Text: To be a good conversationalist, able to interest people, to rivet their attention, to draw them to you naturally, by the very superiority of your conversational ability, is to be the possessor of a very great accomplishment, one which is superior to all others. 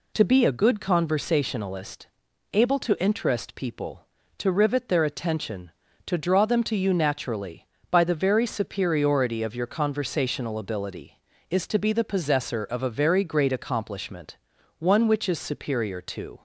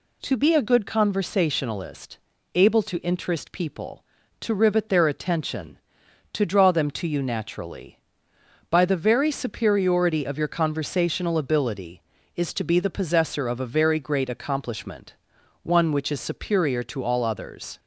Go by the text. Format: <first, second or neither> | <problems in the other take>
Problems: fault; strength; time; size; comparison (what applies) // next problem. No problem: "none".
second | stops before "all others"; at 16.3 s